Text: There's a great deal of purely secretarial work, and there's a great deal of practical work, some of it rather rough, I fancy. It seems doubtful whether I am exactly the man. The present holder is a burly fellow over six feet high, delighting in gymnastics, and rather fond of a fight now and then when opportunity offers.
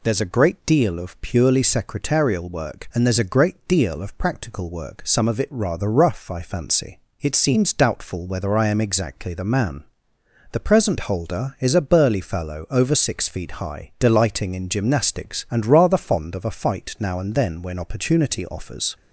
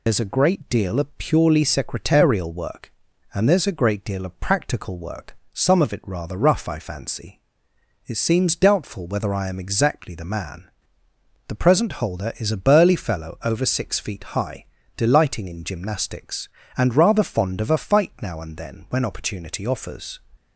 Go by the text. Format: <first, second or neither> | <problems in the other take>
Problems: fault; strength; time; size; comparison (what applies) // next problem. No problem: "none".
first | loses the start of "There's"; at 0.0 s; 70 ms // pauses between "feet" and "high"; slight; at 14.2 s; 0.16 s long